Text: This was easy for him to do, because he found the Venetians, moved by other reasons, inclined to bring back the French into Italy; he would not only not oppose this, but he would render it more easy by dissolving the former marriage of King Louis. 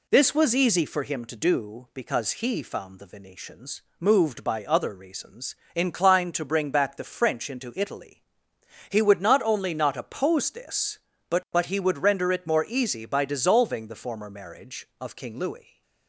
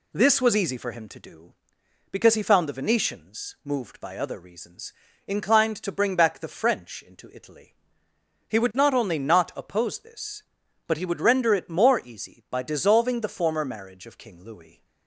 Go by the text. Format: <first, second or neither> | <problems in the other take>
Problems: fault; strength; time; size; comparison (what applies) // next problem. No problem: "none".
second | says "but" twice; at 11.5 s